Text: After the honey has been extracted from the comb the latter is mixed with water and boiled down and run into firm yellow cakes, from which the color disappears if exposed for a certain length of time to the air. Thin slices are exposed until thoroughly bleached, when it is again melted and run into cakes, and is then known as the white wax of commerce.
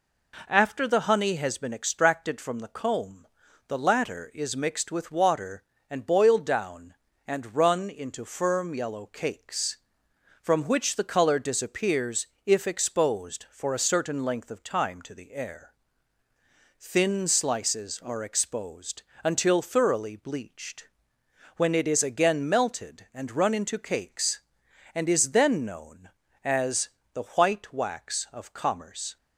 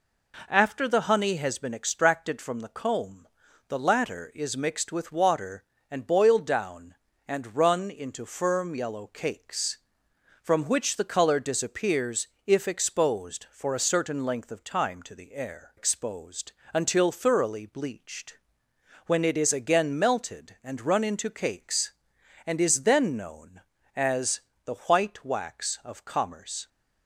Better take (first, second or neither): first